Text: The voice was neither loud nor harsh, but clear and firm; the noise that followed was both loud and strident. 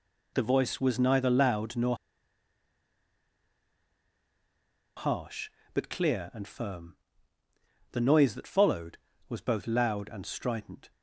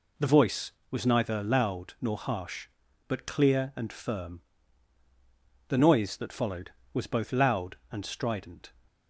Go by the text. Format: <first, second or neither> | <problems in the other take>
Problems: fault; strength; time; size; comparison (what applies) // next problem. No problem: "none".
second | pauses between "nor" and "harsh"; strong; at 1.9 s; 3.0 s long